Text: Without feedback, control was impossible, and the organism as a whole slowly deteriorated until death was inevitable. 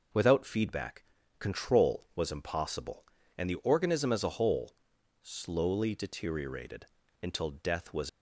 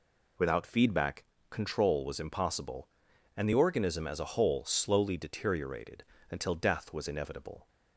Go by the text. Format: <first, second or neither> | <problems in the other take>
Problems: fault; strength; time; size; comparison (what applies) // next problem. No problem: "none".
second | pauses between "whole" and "slowly"; noticeable; at 4.7 s; 0.48 s long // pauses between "deteriorated" and "until"; slight; at 6.8 s; 0.36 s long; slight in the second // stops before "inevitable"; at 8.0 s